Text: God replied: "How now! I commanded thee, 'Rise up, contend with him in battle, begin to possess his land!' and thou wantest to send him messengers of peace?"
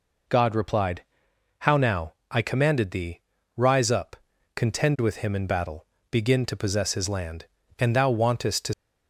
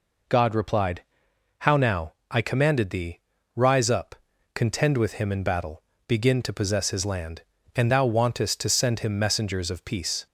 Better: second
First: stops before "send him messengers of peace"; at 8.7 s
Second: none

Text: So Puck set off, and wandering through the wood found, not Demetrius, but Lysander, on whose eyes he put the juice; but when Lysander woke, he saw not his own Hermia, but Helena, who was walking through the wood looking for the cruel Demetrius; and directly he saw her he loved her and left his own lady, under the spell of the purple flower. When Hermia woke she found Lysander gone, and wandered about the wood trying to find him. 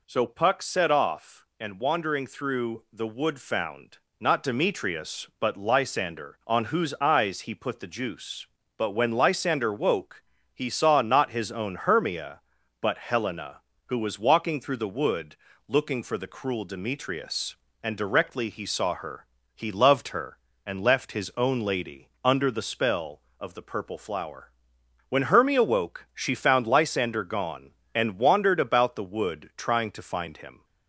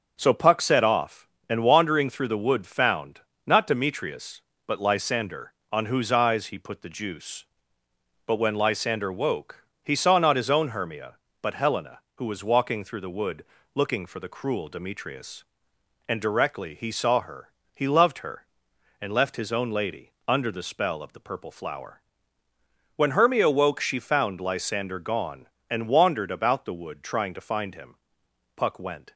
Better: first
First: pauses between "wood" and "looking"; slight; at 15.3 s; 0.32 s long // pauses between "her" and "he"; slight; at 19.2 s; 0.30 s long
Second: starts louder than the rest; until 1.1 s; 6.5 dB // pauses between "wood" and "looking"; slight; at 13.4 s; 0.30 s long // pauses between "her" and "he"; slight; at 17.4 s; 0.26 s long // goes on to say "Puck went"; from 28.5 s on; 0.58 s long

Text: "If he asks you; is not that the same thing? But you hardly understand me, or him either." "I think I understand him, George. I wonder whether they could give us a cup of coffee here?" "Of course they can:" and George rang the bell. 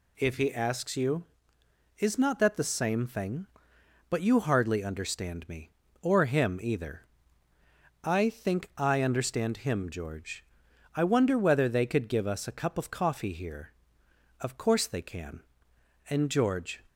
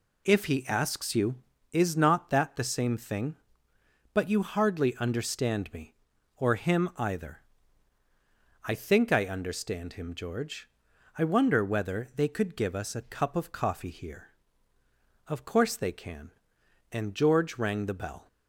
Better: second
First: stops before "rang the bell"; at 16.8 s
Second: none

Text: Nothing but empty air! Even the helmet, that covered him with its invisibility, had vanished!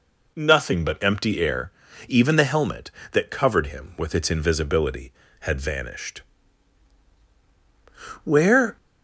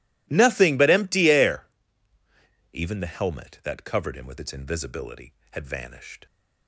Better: second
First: goes on to say "Where"; from 8.2 s on; 0.52 s long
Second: none

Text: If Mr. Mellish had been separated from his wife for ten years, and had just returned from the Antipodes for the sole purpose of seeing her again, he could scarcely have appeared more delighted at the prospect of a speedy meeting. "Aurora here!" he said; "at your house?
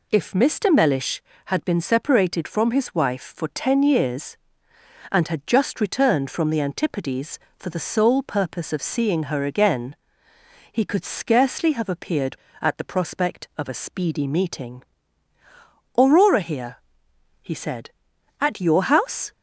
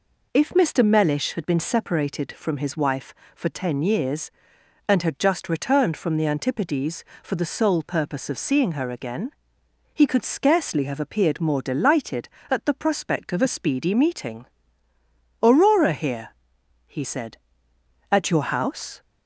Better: second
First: skips "more delighted"; at 12.4 s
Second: none

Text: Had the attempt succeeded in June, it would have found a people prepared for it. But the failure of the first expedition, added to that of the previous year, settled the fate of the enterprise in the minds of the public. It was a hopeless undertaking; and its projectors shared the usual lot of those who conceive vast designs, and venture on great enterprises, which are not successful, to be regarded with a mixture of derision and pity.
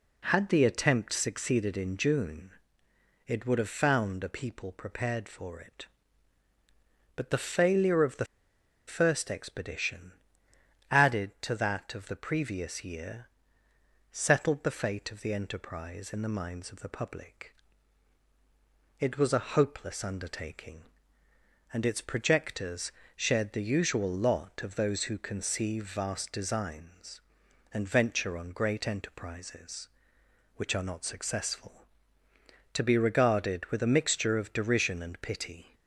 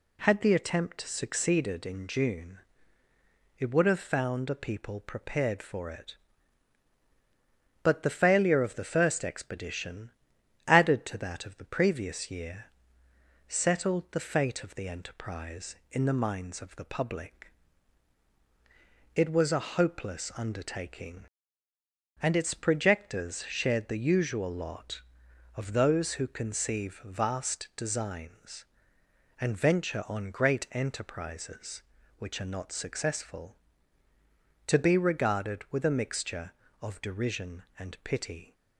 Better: second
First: pauses between "the" and "first"; noticeable; at 8.2 s; 0.61 s long // pauses between "projectors" and "shared"; slight; at 22.9 s; 0.26 s long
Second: none

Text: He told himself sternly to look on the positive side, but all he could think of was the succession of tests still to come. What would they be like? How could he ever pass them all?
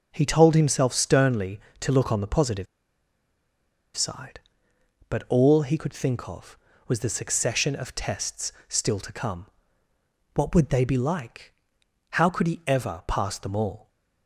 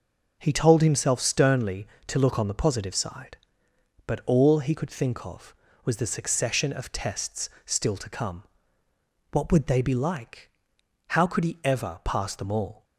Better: second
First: pauses between "positive" and "side"; strong; at 2.6 s; 1.2 s long // pauses between "tests" and "still"; slight; at 8.5 s; 0.16 s long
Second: pauses between "tests" and "still"; slight; at 7.4 s; 0.16 s long

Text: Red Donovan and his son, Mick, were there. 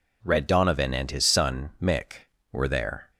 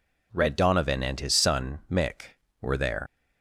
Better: first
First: none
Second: leaves "there" unfinished; at 3.0 s; 130 ms

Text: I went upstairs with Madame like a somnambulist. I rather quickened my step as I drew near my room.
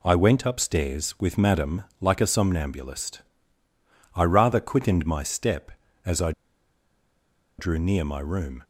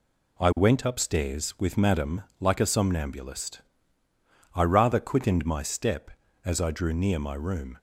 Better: second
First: pauses between "Madame" and "like"; slight; at 1.8 s; 0.18 s long // pauses between "I" and "drew"; strong; at 6.3 s; 1.2 s long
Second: pauses between "Madame" and "like"; slight; at 2.2 s; 0.18 s long

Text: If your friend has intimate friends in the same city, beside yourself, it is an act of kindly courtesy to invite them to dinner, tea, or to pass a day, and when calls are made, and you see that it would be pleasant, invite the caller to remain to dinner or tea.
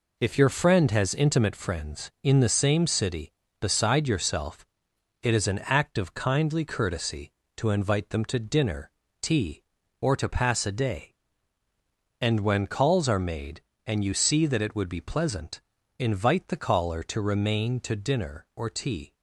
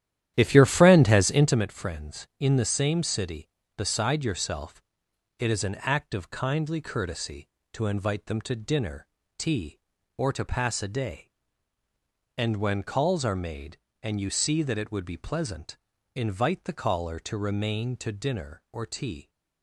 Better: first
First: none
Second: starts louder than the rest; strong; until 1.6 s; 11 dB

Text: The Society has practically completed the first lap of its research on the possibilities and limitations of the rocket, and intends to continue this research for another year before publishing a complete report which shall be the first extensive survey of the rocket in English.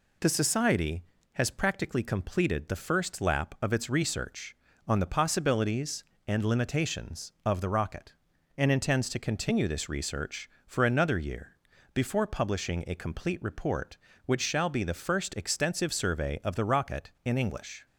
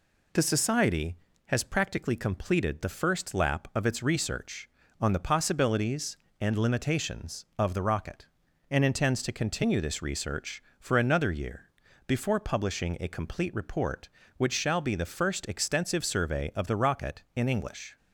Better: neither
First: pauses between "year" and "before"; slight; at 11.5 s; 0.36 s long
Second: pauses between "year" and "before"; slight; at 11.6 s; 0.36 s long

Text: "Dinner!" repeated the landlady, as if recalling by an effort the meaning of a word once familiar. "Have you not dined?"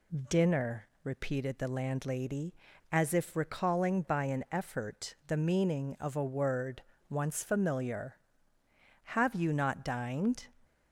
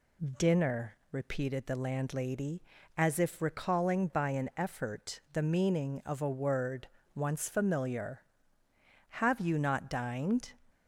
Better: neither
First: pauses between "word" and "once"; slight; at 6.8 s; 0.26 s long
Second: pauses between "word" and "once"; slight; at 6.8 s; 0.26 s long

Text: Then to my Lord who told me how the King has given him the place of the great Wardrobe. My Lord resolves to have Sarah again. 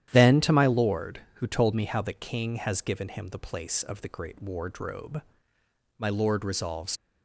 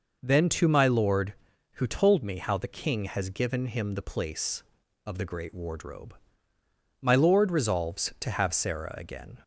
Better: second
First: starts louder than the rest; strong; until 1.1 s; 11 dB // stops before "to have Sarah again"; at 6.9 s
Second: none

